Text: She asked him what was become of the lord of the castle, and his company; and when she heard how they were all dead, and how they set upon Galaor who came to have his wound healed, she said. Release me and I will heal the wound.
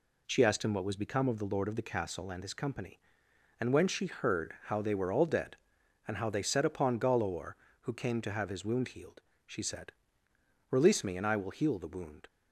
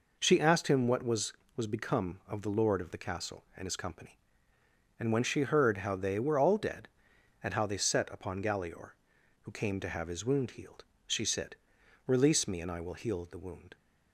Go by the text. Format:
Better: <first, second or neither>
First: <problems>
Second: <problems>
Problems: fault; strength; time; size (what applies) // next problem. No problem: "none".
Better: first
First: none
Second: says "was" twice; at 1.5 s